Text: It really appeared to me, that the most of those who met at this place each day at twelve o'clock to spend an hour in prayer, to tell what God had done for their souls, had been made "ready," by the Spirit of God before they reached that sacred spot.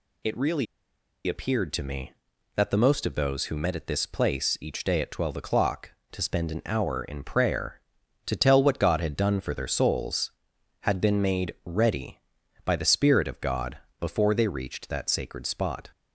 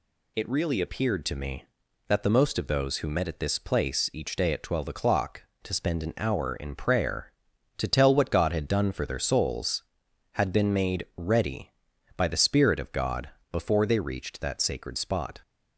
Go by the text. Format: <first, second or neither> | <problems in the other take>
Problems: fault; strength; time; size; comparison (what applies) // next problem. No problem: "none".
second | pauses between "really" and "appeared"; noticeable; at 0.6 s; 0.62 s long // pauses between "God" and "before"; slight; at 13.7 s; 0.22 s long; slight in the second